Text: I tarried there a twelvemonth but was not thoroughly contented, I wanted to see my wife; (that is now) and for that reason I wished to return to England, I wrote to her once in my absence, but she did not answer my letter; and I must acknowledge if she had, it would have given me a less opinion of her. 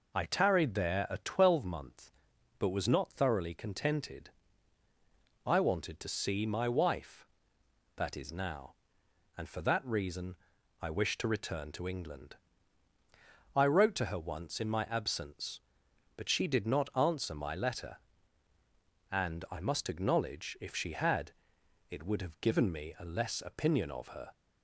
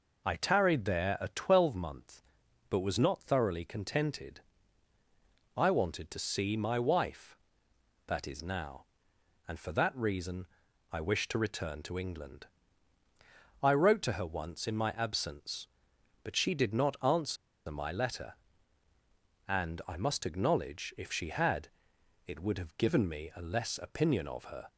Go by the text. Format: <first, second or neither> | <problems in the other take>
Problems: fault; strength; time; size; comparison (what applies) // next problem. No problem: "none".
first | pauses between "reason" and "I"; noticeable; at 10.4 s; 0.46 s long; noticeable in the first // pauses between "answer" and "my"; slight; at 17.3 s; 0.32 s long